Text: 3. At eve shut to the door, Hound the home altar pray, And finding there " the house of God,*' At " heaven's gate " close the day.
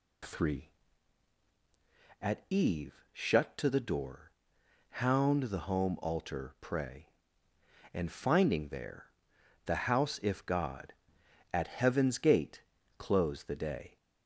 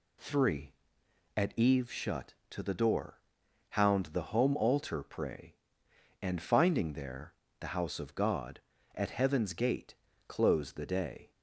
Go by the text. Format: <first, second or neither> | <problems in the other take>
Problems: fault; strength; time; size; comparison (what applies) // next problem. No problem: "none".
second | says "if" for "of"; at 10.2 s